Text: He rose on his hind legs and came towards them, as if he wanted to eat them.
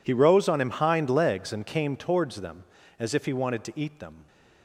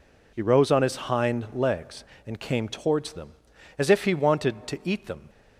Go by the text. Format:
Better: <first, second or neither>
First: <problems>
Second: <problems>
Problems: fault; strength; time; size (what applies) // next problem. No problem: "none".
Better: second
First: says "him" for "his"; at 0.6 s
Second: none